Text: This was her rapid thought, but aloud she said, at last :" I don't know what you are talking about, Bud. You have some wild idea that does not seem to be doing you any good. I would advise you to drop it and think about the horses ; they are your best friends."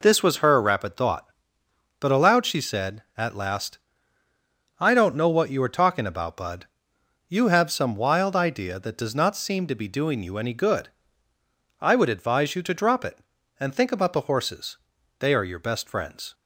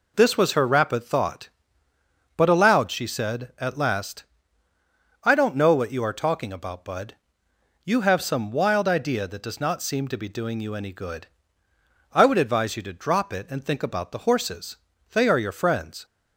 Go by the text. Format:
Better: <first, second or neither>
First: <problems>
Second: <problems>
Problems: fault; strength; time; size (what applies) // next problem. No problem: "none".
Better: first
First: none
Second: skips "best"; at 15.5 s